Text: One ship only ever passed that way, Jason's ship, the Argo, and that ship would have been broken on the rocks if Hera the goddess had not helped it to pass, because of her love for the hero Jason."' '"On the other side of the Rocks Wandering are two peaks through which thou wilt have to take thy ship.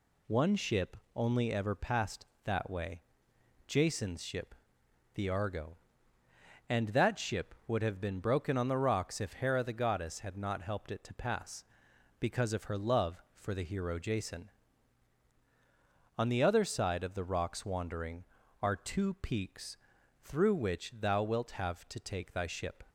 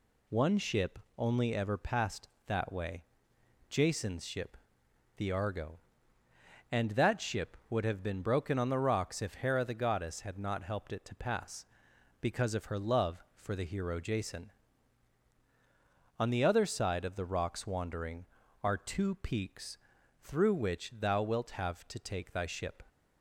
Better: neither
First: pauses between "ship" and "only"; slight; at 0.9 s; 0.18 s long // pauses between "peaks" and "through"; at 19.7 s; 0.45 s long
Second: pauses between "ship" and "only"; slight; at 0.9 s; 0.18 s long // pauses between "peaks" and "through"; at 19.7 s; 0.44 s long

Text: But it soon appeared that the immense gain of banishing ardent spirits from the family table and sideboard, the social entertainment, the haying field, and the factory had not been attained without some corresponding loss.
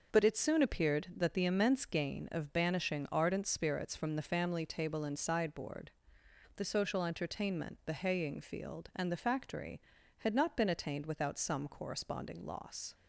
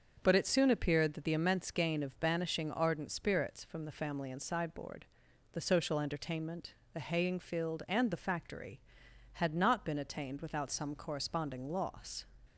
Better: first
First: starts louder than the rest; noticeable; until 1.2 s; 6 dB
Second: starts louder than the rest; until 1.2 s; 6.5 dB // skips "table"; at 4.2 s

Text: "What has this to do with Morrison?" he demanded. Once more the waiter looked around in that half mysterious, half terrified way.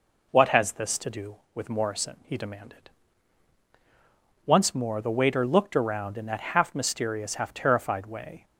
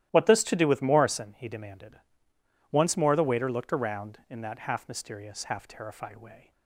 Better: first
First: none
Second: starts louder than the rest; strong; until 1.1 s; 13.5 dB // skips "has"; at 0.2 s

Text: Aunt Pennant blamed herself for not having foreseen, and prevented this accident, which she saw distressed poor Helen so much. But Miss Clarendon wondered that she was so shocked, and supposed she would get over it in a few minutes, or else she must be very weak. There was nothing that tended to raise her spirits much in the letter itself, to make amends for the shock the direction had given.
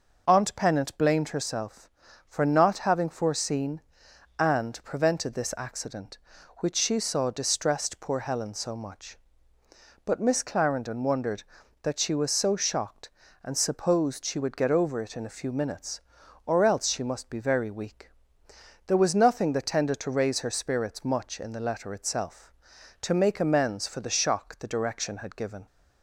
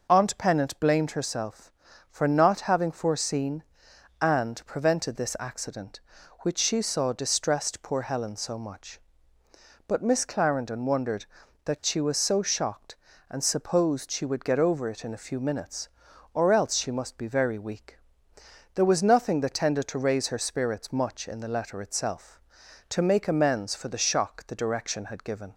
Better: neither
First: none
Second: none

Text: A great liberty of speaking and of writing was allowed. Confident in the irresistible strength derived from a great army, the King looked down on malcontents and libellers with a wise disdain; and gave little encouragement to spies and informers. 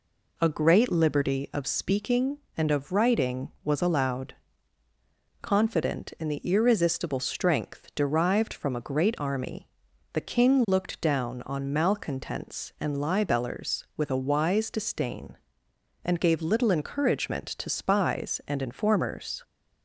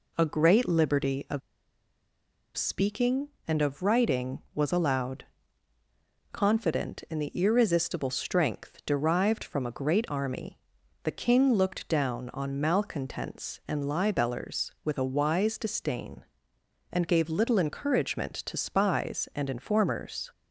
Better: first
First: none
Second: pauses between "of" and "speaking"; at 1.4 s; 1.1 s long

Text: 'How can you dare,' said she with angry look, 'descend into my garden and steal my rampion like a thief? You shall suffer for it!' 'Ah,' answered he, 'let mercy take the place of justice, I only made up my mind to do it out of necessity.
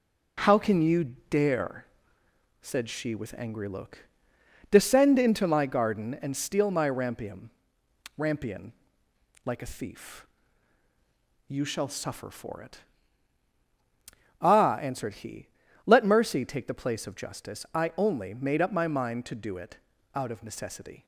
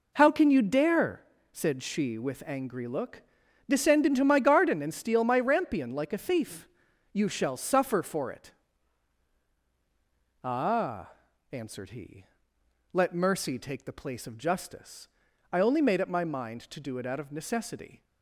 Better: second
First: says "rampion" twice; at 8.1 s // pauses between "it" and "out"; slight; at 19.7 s; 0.36 s long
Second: none

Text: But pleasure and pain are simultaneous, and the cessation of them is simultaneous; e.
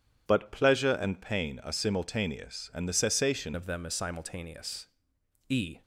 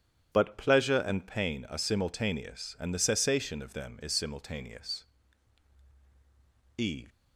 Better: second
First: changes voice at "of"; from 3.5 s on; 2.3 s long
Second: none

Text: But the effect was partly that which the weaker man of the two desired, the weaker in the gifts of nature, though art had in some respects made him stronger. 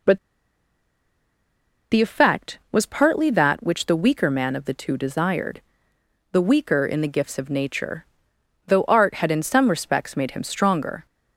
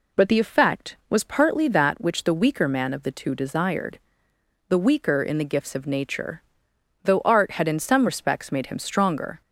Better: second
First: pauses between "But" and "the"; strong; at 0.1 s; 1.7 s long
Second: none

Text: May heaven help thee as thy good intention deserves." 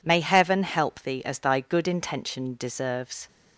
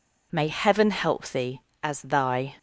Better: first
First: none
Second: stops before "good intention deserves"; at 2.5 s

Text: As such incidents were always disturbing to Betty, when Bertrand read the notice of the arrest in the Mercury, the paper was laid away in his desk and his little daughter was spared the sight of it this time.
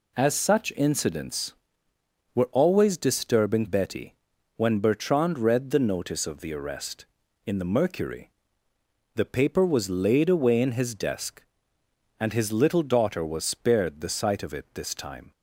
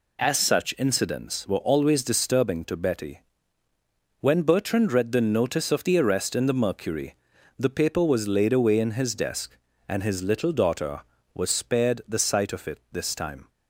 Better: second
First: skips "to"; at 3.6 s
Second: none

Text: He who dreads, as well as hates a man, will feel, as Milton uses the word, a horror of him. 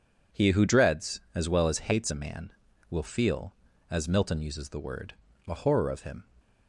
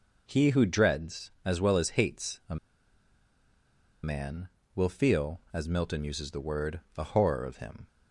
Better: first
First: none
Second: pauses between "a" and "man"; strong; at 2.5 s; 1.4 s long

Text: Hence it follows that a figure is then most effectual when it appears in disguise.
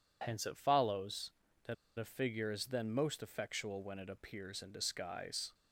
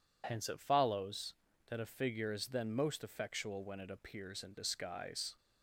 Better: second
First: pauses between "that" and "a"; slight; at 1.7 s; 0.23 s long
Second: none

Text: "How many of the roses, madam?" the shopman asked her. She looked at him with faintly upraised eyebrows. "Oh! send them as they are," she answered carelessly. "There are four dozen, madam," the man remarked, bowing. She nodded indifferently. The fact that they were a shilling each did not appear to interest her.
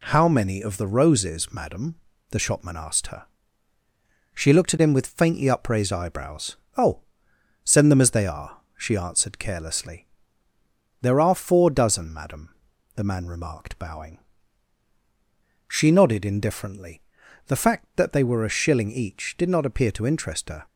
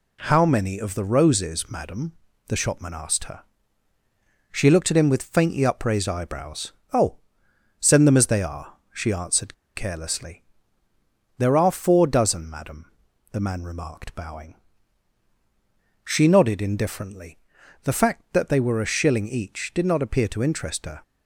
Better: first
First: none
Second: pauses between "answered" and "carelessly"; slight; at 9.5 s; 0.21 s long

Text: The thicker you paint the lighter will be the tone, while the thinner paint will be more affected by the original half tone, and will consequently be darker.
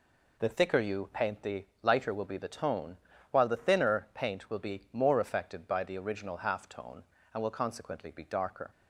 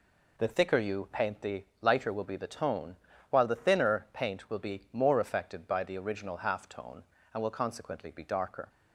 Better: neither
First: pauses between "the" and "lighter"; slight; at 1.6 s; 0.16 s long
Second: pauses between "the" and "lighter"; slight; at 1.6 s; 0.16 s long

